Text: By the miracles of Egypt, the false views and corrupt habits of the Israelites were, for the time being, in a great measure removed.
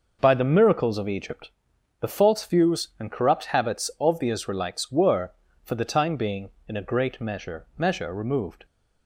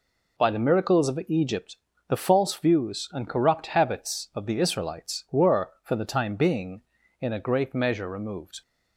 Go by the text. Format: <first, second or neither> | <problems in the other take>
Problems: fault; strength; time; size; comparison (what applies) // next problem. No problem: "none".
second | says "measure" twice; at 7.7 s